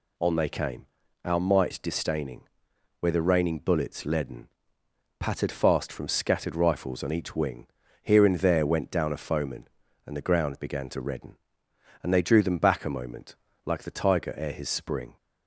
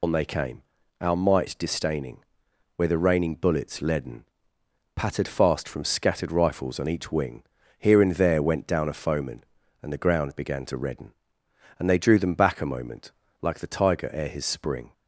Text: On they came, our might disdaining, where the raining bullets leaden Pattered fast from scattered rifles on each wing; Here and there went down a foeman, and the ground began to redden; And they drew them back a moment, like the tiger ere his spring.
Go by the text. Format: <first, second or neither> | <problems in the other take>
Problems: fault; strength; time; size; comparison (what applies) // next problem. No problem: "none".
first | loses the start of "On"; at 0.0 s; 85 ms // pauses between "leaden" and "Pattered"; noticeable; at 4.2 s; 0.70 s long; noticeable in the first